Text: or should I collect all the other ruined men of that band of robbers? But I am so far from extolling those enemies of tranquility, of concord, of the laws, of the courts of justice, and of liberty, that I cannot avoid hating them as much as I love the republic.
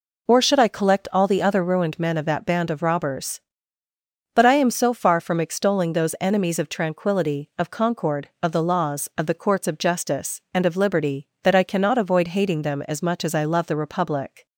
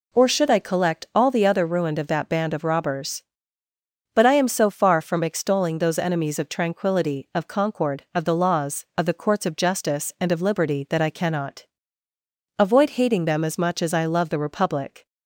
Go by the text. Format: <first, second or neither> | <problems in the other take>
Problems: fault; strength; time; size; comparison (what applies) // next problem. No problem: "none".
first | skips "men"; at 1.9 s // pauses between "cannot" and "avoid"; noticeable; at 11.6 s; 0.92 s long